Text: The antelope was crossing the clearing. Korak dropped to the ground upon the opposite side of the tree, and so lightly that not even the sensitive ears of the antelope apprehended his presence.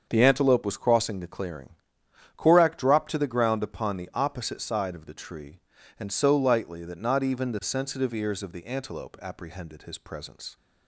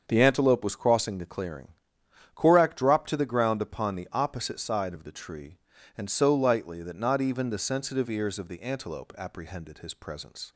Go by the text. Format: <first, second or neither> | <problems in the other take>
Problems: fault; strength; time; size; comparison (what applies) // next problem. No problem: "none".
neither | starts louder than the rest; the same in both